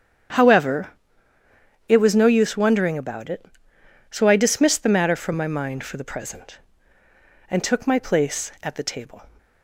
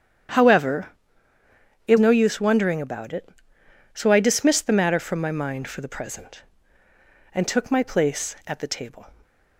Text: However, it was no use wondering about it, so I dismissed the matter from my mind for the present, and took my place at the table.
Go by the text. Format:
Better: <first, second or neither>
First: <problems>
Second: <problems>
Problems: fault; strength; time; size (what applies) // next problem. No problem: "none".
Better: first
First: starts louder than the rest; strong; until 2.2 s; 8.5 dB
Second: starts louder than the rest; strong; until 2.3 s; 9.5 dB // skips "was"; at 1.9 s